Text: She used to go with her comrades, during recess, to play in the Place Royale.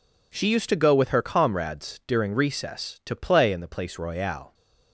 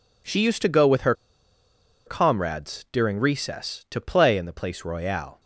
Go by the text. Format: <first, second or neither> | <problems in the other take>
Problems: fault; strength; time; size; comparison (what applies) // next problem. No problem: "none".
first | pauses between "her" and "comrades"; noticeable; at 1.1 s; 0.92 s long